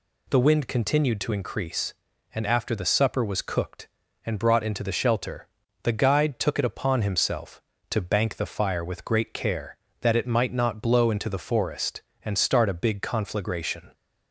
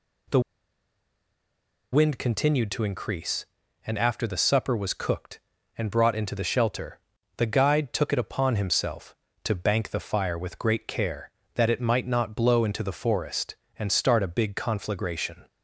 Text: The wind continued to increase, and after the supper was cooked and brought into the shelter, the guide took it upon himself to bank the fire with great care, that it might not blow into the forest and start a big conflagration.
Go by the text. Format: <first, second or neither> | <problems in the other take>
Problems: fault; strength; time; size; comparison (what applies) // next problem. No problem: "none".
first | pauses between "The" and "wind"; strong; at 0.4 s; 1.5 s long